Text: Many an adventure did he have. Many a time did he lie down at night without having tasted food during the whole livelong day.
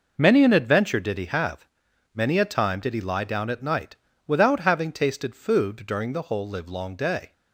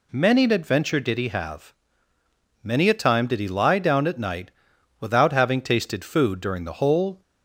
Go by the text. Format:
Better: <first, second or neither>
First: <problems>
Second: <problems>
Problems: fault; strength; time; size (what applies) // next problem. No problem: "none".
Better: first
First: pauses between "night" and "without"; slight; at 3.9 s; 0.30 s long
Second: pauses between "night" and "without"; noticeable; at 4.5 s; 0.50 s long // stops before "livelong day"; at 7.2 s